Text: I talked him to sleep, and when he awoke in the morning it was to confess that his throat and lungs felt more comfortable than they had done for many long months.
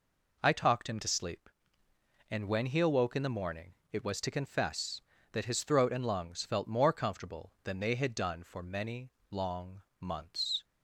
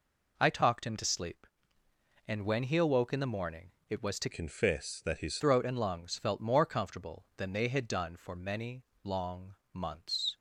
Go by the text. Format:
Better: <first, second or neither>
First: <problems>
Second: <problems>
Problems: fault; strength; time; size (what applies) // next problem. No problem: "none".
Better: first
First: pauses between "morning" and "it"; slight; at 3.7 s; 0.16 s long // pauses between "many" and "long"; slight; at 9.1 s; 0.18 s long // pauses between "long" and "months"; slight; at 9.8 s; 0.16 s long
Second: pauses between "morning" and "it"; slight; at 3.7 s; 0.16 s long // changes voice from "confess" to "his"; from 4.3 to 5.3 s; 1.0 s long // pauses between "many" and "long"; slight; at 8.8 s; 0.18 s long // pauses between "long" and "months"; slight; at 9.5 s; 0.16 s long